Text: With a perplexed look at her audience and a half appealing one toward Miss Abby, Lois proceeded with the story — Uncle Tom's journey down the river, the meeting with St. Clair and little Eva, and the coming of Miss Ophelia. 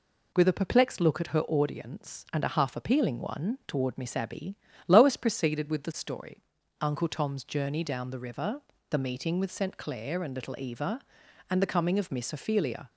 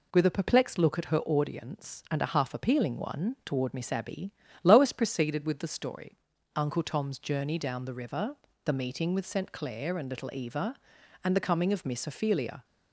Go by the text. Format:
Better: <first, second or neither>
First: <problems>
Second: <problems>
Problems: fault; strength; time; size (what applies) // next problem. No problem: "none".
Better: neither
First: none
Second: none